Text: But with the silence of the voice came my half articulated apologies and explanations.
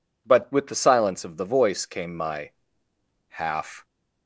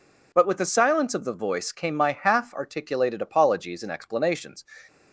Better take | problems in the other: second | pauses between "my" and "half"; noticeable; at 2.5 s; 0.78 s long // stops before "articulated apologies and explanations"; at 3.8 s

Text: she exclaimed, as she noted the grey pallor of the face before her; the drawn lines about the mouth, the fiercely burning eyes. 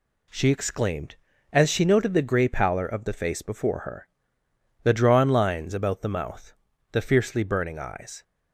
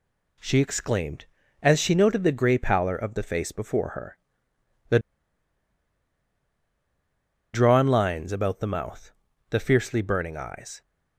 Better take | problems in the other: first | pauses between "the" and "drawn"; strong; at 4.9 s; 2.5 s long

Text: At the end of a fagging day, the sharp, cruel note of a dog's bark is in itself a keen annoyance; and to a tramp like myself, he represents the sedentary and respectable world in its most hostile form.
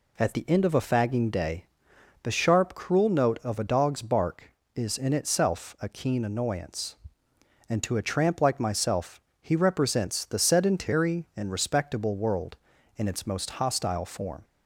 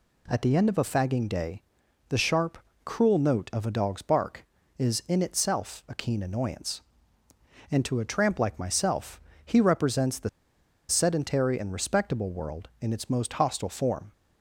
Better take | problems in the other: first | pauses between "the" and "sedentary"; noticeable; at 10.2 s; 0.60 s long

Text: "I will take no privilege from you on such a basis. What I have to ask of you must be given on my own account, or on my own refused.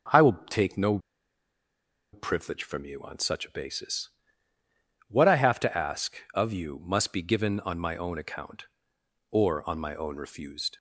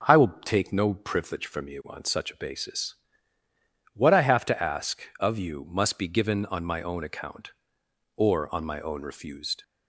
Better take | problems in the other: second | starts louder than the rest; until 2.3 s; 6.5 dB; also in the second // pauses between "no" and "privilege"; at 0.9 s; 1.1 s long

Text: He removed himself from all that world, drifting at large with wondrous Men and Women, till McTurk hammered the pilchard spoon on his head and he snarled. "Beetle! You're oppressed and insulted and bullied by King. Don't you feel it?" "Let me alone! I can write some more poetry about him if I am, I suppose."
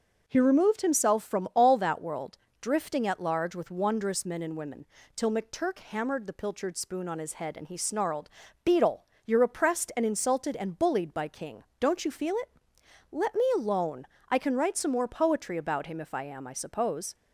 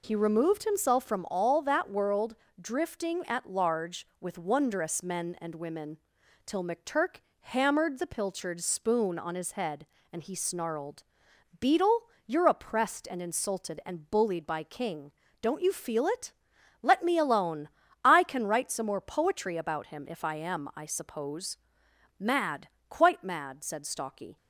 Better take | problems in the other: first | pauses between "McTurk" and "hammered"; slight; at 7.2 s; 0.20 s long // goes on to say "Mad Quite mad said Stalky"; strong; from 22.1 s on; 2.1 s long

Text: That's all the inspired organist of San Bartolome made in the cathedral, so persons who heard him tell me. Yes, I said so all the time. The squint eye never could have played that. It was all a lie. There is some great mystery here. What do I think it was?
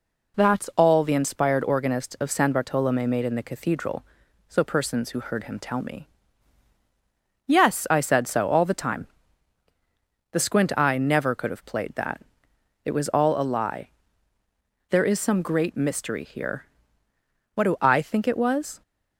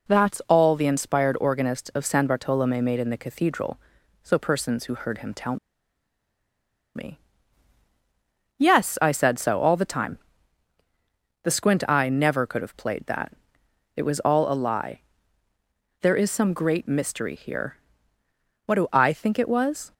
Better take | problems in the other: first | pauses between "tell" and "me"; strong; at 5.5 s; 1.3 s long

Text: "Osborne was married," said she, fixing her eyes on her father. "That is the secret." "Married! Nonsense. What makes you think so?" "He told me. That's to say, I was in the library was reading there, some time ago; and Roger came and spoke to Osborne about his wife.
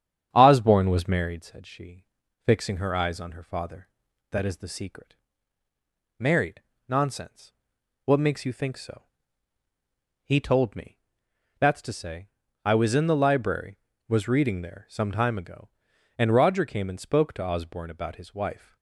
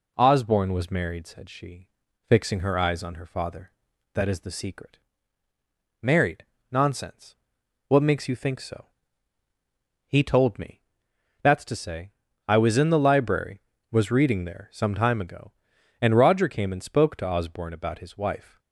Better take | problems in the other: second | starts louder than the rest; strong; until 1.4 s; 9 dB

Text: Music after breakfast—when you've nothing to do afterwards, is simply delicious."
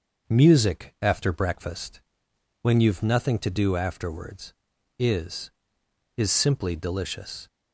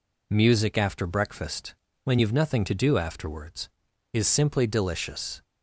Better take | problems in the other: second | starts louder than the rest; until 1.4 s; 6 dB // says "is" twice; at 6.1 s

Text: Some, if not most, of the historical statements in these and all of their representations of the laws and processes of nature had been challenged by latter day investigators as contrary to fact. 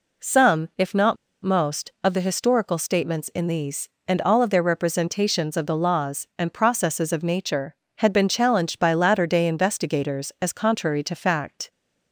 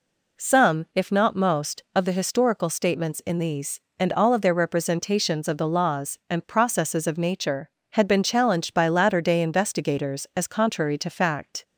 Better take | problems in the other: second | pauses between "not" and "most"; slight; at 1.1 s; 0.27 s long

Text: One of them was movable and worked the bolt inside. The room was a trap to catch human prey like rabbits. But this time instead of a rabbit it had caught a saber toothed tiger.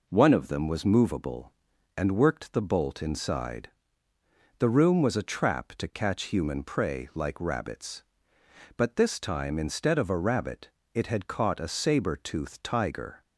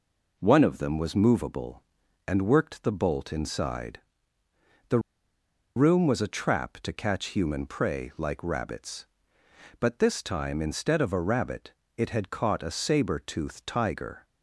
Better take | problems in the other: first | pauses between "The" and "room"; noticeable; at 4.9 s; 0.76 s long // pauses between "rabbit" and "it"; slight; at 11.7 s; 0.26 s long; slight in the first

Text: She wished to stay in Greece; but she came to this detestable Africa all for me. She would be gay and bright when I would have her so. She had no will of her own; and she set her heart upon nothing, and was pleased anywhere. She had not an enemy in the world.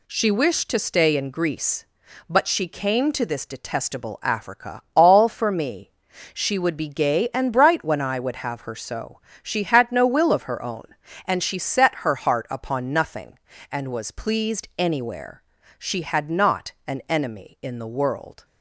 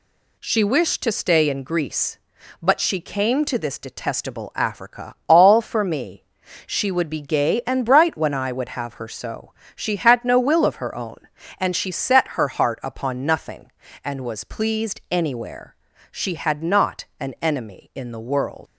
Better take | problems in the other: first | leaves "world" unfinished; at 18.6 s; 115 ms

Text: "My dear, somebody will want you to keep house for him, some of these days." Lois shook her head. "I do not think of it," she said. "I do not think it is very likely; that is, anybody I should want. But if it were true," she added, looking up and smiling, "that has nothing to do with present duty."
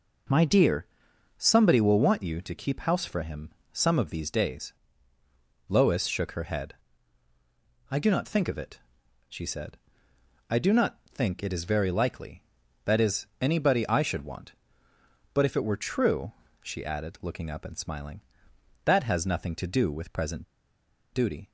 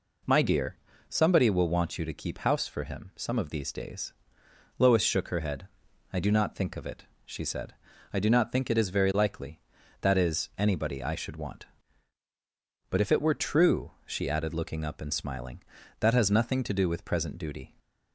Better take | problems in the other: second | pauses between "present" and "duty"; noticeable; at 20.4 s; 0.68 s long

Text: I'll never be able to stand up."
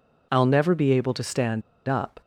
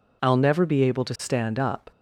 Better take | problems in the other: second | pauses between "stand" and "up"; slight; at 1.6 s; 0.26 s long

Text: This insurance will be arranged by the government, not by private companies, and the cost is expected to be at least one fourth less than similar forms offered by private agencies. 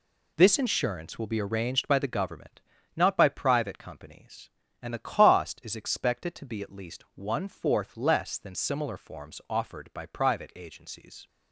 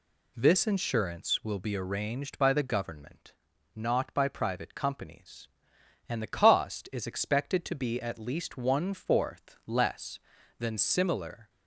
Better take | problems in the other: first | stops before "forms offered by private agencies"; at 11.4 s

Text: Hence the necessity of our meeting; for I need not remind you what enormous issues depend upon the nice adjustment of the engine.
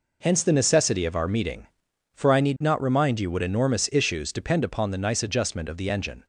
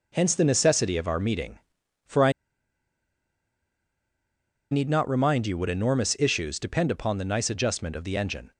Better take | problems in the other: first | pauses between "I" and "need"; strong; at 2.3 s; 2.3 s long

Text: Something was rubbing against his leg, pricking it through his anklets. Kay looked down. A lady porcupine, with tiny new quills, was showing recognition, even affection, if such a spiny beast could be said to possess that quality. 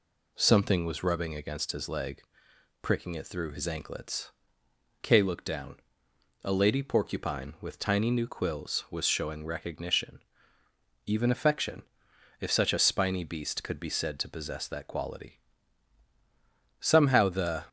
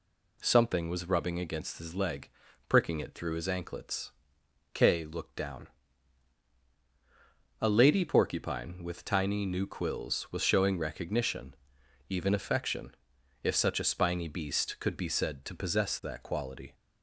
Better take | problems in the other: second | goes on to say "Somehow the"; noticeable; from 16.7 s on; 0.86 s long

